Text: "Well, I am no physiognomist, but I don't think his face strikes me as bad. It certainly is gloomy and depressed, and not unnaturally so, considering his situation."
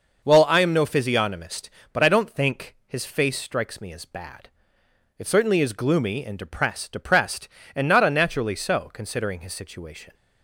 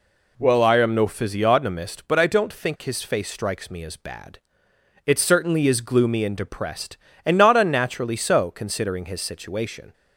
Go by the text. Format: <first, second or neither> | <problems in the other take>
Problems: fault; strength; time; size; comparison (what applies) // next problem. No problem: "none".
second | starts louder than the rest; noticeable; until 1.2 s; 6 dB // says "depressed" twice; at 6.9 s